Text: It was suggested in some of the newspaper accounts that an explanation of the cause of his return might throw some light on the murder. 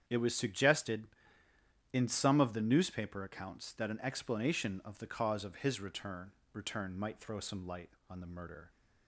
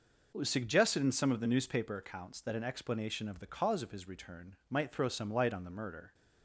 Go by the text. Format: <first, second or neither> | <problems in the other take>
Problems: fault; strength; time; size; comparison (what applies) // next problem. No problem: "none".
second | starts louder than the rest; strong; until 1.0 s; 8.5 dB // says "return" twice; at 6.5 s